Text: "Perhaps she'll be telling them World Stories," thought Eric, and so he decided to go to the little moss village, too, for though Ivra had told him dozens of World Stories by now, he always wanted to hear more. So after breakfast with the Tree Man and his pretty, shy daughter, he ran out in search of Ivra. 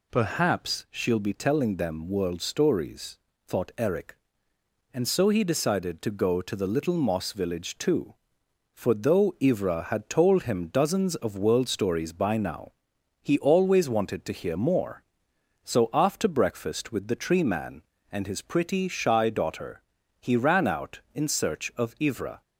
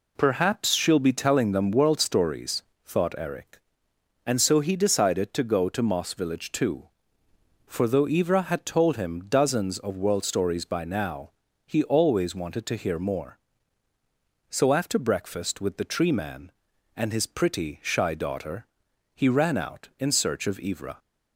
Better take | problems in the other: first | skips "the little"; at 5.8 s

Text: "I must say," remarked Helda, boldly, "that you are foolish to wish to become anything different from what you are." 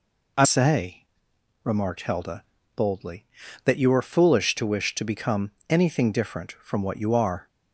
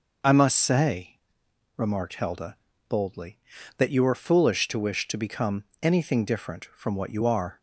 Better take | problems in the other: second | skips "must"; at 0.4 s // pauses between "become" and "anything"; slight; at 5.4 s; 0.18 s long; slight in the second

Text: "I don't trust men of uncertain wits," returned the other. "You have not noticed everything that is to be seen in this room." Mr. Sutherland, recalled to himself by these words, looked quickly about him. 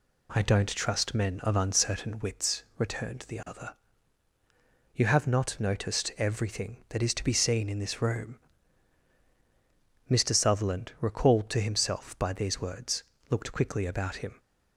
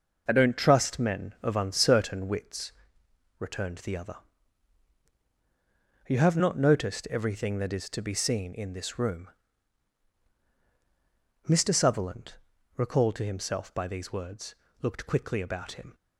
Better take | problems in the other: neither | none

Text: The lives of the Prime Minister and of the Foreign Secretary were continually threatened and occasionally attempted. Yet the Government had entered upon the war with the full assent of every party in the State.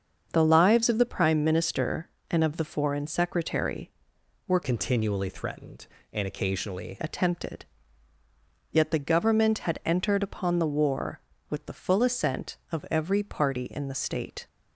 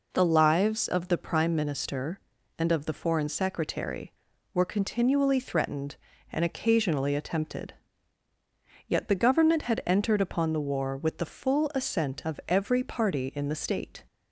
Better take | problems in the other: second | starts louder than the rest; until 1.3 s; 7 dB // changes voice from "continually" to "occasionally"; from 4.6 to 6.9 s; 2.3 s long

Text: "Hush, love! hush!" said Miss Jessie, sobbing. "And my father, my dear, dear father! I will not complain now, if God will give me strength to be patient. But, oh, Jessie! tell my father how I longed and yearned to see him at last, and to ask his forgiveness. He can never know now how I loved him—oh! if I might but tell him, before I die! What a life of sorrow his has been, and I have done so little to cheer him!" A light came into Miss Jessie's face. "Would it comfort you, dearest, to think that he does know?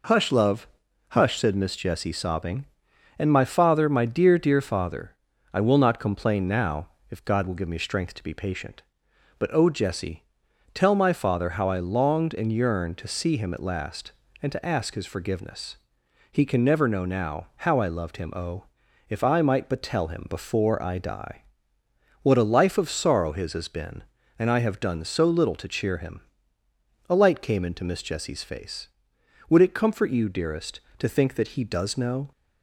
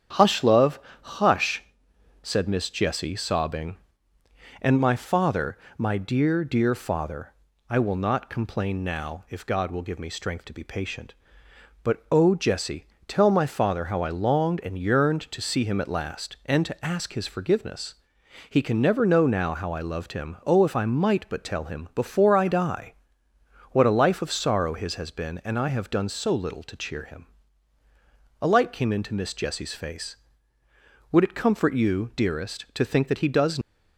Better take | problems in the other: first | starts louder than the rest; strong; until 1.4 s; 8.5 dB // stops before "know"; at 33.6 s

